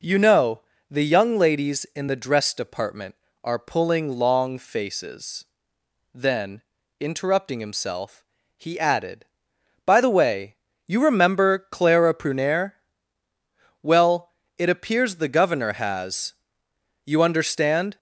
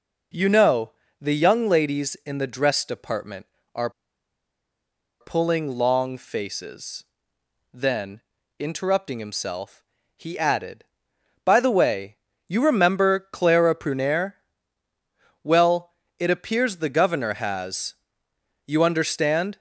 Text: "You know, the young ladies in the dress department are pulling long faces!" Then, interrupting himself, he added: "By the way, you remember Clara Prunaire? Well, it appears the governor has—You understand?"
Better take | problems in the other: first | pauses between "are" and "pulling"; strong; at 3.9 s; 1.3 s long

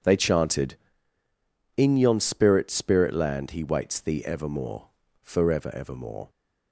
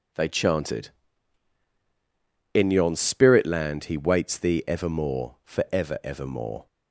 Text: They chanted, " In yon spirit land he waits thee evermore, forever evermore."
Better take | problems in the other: second | says "spirit" twice; at 2.6 s

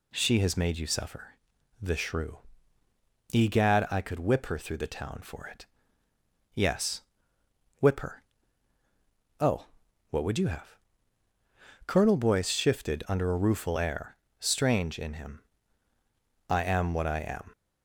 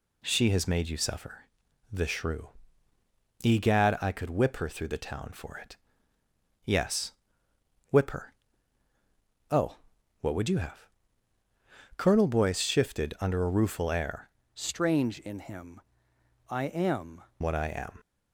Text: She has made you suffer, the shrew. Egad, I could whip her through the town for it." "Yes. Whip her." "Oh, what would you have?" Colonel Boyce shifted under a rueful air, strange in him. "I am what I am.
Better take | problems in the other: first | changes voice from "strange" to "am"; from 14.5 to 17.2 s; 2.7 s long

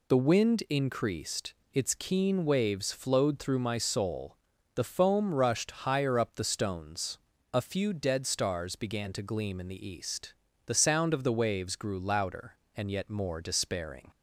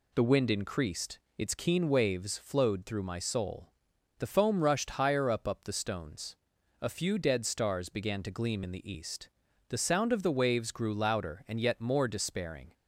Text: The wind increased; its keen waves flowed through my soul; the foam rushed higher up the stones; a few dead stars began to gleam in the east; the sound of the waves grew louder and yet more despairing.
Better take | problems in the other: first | says "up" twice; at 5.4 s

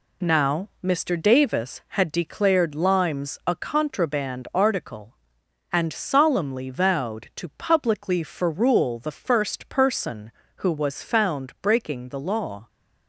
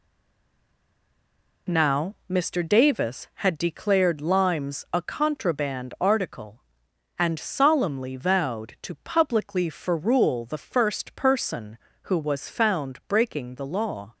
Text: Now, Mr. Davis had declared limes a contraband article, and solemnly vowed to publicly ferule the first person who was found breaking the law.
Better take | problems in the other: first | stays silent before the first word; noticeable; until 1.6 s; 1.6 s long

